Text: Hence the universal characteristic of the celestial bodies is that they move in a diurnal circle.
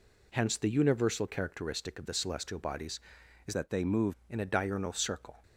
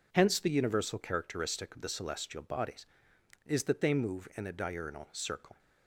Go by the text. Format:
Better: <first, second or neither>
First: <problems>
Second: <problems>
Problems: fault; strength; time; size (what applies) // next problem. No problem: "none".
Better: second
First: changes voice from "that" to "move"; from 3.5 to 4.1 s; 0.6 s long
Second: none